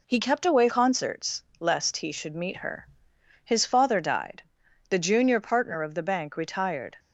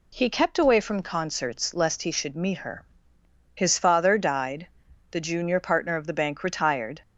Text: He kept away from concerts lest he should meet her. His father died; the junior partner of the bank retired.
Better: second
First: skips "from"; at 0.6 s // pauses between "concerts" and "lest"; slight; at 1.4 s; 0.16 s long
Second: none

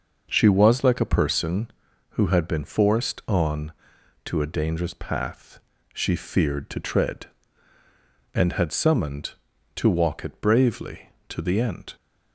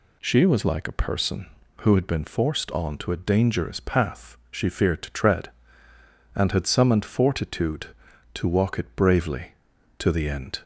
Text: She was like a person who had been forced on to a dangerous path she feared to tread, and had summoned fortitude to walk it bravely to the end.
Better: second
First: pauses between "path" and "she"; slight; at 5.5 s; 0.32 s long // skips "fortitude"; at 9.5 s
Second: none

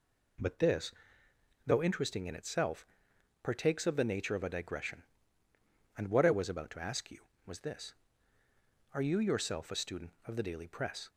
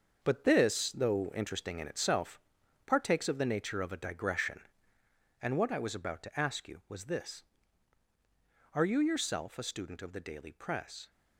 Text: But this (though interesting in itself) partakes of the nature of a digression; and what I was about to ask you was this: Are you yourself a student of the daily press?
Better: first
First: none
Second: gets quieter; strong; throughout; 9 dB

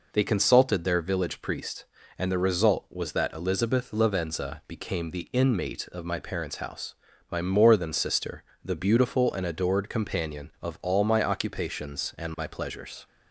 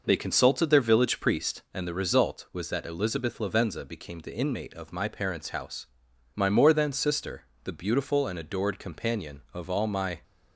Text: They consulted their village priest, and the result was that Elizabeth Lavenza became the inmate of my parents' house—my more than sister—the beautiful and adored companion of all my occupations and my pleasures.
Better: first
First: none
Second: stops before "occupations and my pleasures"; at 10.2 s

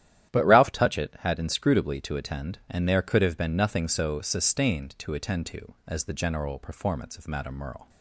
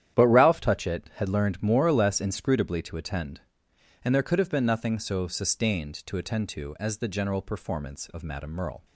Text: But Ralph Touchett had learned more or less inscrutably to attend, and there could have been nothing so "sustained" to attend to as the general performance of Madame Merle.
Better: second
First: starts louder than the rest; strong; until 1.3 s; 11.5 dB // skips "learned more or less"; at 1.3 s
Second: starts louder than the rest; strong; until 1.2 s; 10.5 dB

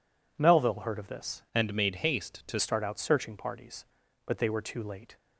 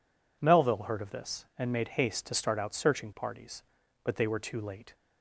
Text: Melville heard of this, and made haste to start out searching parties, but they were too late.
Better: second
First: changes voice from "and" to "to"; from 1.5 to 2.6 s; 1.1 s long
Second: none

